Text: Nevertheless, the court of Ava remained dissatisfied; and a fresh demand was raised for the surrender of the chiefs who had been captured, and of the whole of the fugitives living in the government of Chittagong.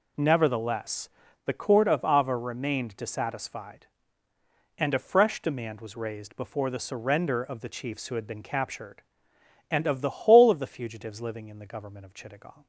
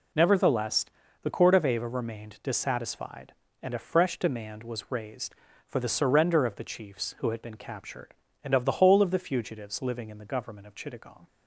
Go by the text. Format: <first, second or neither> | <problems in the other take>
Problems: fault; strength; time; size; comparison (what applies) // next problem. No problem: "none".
second | says "before" for "for"; at 6.3 s